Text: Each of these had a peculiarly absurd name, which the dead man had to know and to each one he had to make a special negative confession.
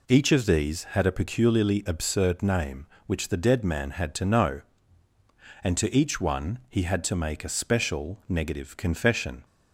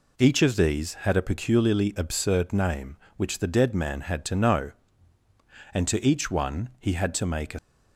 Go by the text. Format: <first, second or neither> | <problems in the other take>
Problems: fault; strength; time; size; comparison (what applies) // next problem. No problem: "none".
first | stops before "special negative confession"; at 7.5 s